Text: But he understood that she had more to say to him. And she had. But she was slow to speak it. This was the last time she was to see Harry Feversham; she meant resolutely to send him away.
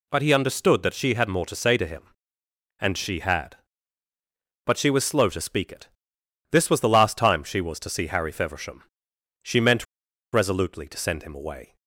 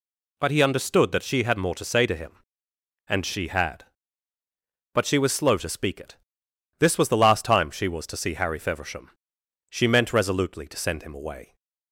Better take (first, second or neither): second